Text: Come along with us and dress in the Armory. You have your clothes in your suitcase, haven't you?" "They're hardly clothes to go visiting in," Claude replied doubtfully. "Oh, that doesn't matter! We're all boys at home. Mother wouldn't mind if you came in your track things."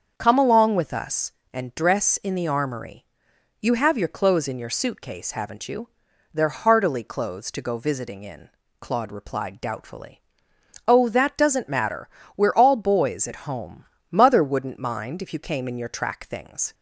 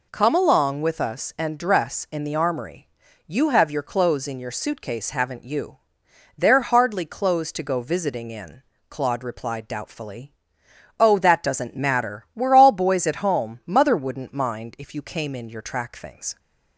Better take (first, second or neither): second